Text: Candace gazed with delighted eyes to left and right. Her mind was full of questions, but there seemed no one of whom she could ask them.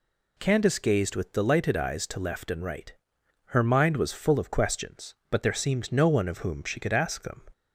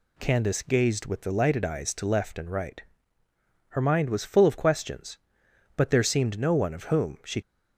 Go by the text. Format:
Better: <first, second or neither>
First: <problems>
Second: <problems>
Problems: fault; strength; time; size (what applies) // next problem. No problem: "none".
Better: first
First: none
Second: stops before "could ask them"; at 7.4 s